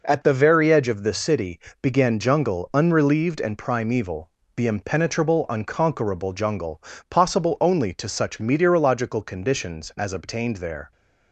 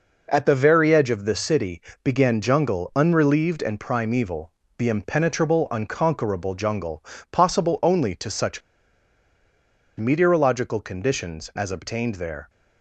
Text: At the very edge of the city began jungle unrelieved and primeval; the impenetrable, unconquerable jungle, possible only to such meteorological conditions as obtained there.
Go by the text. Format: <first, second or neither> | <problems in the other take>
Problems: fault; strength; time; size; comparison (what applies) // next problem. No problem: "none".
first | pauses between "city" and "began"; slight; at 1.8 s; 0.22 s long; slight in the first // pauses between "such" and "meteorological"; strong; at 8.6 s; 1.3 s long